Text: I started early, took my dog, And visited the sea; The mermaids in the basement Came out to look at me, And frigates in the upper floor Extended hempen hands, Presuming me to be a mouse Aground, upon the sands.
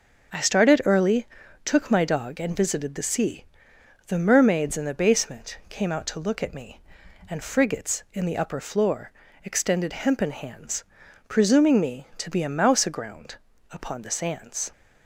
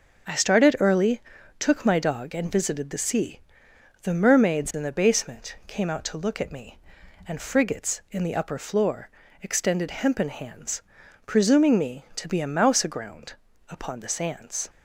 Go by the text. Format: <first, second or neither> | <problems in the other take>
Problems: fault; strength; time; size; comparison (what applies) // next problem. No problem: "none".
neither | starts louder than the rest; the same in both // pauses between "floor" and "Extended"; slight; the same in both